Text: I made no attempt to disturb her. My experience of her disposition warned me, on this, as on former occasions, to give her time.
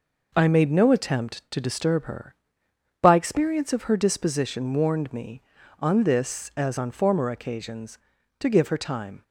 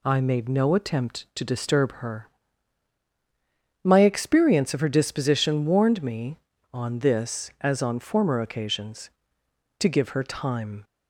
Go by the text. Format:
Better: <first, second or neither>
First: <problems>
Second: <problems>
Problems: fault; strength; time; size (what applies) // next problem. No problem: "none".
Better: second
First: says "By" for "My"; at 3.0 s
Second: none